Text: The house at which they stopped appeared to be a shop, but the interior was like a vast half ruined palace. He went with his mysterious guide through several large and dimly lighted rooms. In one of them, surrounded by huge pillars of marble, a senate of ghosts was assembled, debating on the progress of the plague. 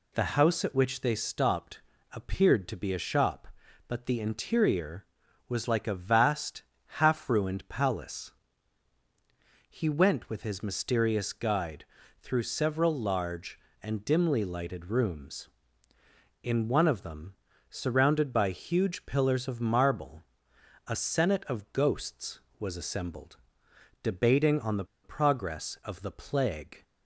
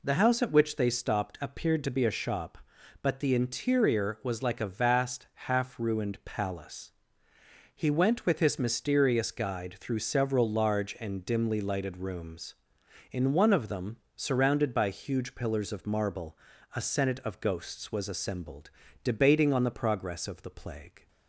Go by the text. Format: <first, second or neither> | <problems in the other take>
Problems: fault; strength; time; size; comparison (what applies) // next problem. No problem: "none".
second | pauses between "stopped" and "appeared"; slight; at 1.8 s; 0.32 s long // pauses between "vast" and "half"; slight; at 6.6 s; 0.32 s long // pauses between "guide" and "through"; at 11.8 s; 0.38 s long // pauses between "the" and "progress"; slight; at 24.8 s; 0.19 s long